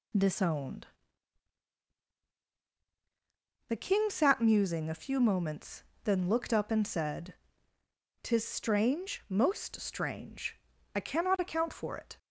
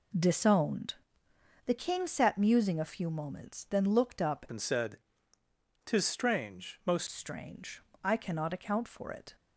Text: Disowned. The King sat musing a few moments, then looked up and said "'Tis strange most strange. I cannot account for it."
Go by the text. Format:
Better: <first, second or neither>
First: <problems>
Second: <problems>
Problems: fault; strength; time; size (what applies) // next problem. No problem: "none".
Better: first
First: pauses between "said" and "Tis"; noticeable; at 7.3 s; 0.90 s long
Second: changes voice from "and" to "most"; from 4.4 to 7.0 s; 2.6 s long // pauses between "said" and "Tis"; noticeable; at 4.9 s; 0.88 s long